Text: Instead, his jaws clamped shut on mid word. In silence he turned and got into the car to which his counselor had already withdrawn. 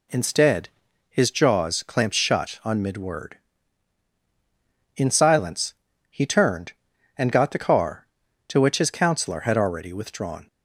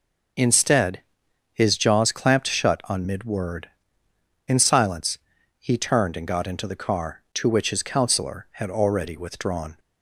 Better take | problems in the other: second | pauses between "silence" and "he"; slight; at 5.7 s; 0.36 s long; also in the second // skips "into"; at 7.5 s

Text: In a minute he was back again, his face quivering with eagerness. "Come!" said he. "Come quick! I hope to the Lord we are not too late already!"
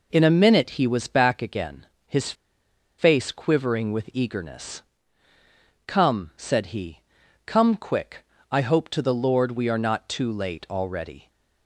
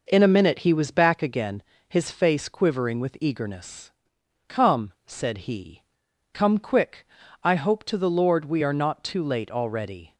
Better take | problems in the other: second | pauses between "his" and "face"; noticeable; at 2.3 s; 0.65 s long

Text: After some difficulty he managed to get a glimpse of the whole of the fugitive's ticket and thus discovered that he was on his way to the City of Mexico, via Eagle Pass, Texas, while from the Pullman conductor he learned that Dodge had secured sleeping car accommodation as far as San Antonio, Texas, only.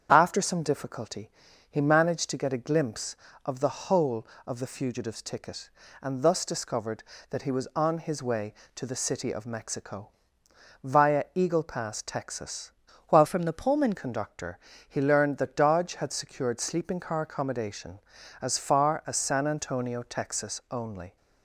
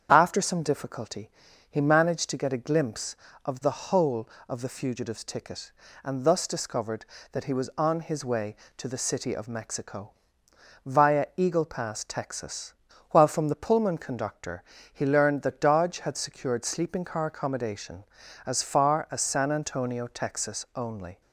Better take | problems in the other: second | starts louder than the rest; strong; until 1.1 s; 8 dB; strong in the second // pauses between "difficulty" and "he"; at 1.3 s; 0.40 s long; also in the second // changes voice from "from" to "Pullman"; from 13.2 to 13.9 s; 0.7 s long // pauses between "conductor" and "he"; slight; at 14.5 s; 0.30 s long; slight in the second

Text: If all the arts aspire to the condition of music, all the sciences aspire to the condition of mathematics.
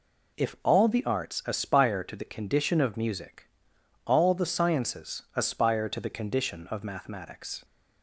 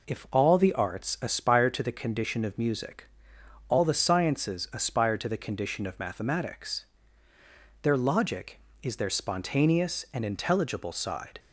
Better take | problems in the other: first | goes on to say "Their logic is their spontaneous and intelligible side"; strong; from 7.8 s on; 3.5 s long

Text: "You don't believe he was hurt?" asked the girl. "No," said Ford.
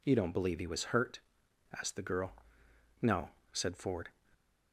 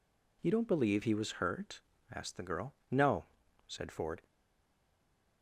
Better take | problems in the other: first | stays silent after the last word; from 4.2 s on; 1.2 s long

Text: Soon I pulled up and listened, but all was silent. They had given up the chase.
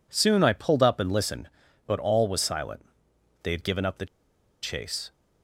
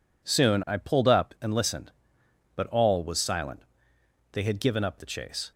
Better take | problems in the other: second | pauses between "the" and "chase"; noticeable; at 4.0 s; 0.56 s long

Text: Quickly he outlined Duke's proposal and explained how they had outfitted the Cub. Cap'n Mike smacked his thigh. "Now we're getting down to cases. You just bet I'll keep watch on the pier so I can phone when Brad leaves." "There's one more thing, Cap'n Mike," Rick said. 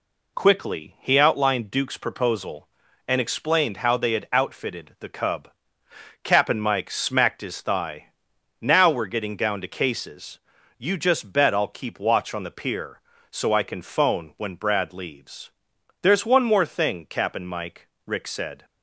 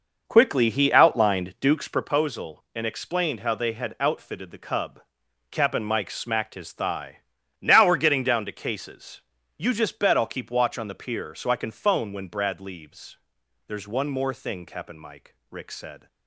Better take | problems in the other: first | starts louder than the rest; noticeable; until 2.2 s; 5.5 dB

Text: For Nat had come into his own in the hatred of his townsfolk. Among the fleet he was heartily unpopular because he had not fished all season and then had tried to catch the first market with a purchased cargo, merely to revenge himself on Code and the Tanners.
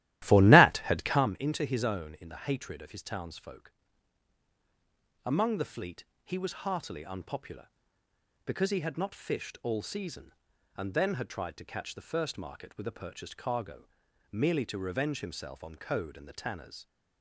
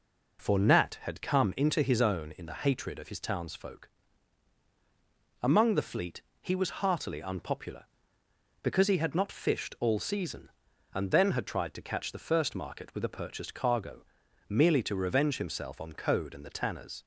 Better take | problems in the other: second | starts louder than the rest; strong; until 1.3 s; 14.5 dB // pauses between "fleet" and "he"; slight; at 6.0 s; 0.18 s long; slight in the second

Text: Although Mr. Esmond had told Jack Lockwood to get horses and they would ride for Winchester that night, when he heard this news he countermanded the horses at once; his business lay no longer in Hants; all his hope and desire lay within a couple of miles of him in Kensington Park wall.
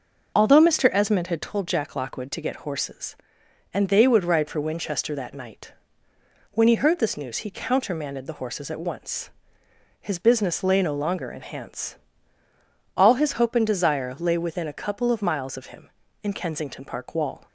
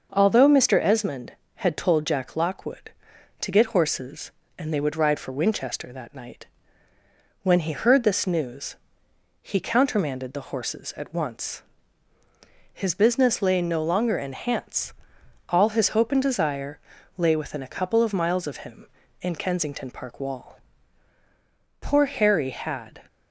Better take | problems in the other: first | starts louder than the rest; until 1.1 s; 6 dB // pauses between "news" and "he"; noticeable; at 8.7 s; 0.66 s long // pauses between "desire" and "lay"; slight; at 16.7 s; 0.36 s long // goes on to say "Poor Harry had"; noticeable; from 21.8 s on; 1.1 s long

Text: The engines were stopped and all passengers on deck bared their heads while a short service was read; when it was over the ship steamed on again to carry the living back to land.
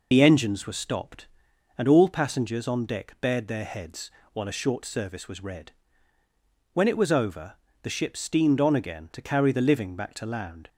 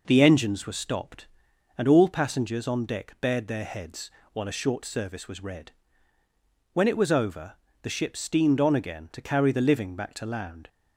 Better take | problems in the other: second | loses the start of "The"; at 0.1 s; 50 ms // pauses between "heads" and "while"; slight; at 4.1 s; 0.22 s long; slight in the second // pauses between "over" and "the"; slight; at 7.5 s; 0.28 s long; slight in the second

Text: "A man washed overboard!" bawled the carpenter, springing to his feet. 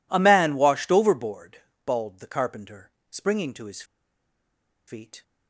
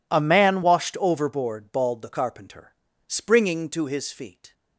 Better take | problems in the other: second | pauses between "his" and "feet"; at 3.8 s; 1.0 s long

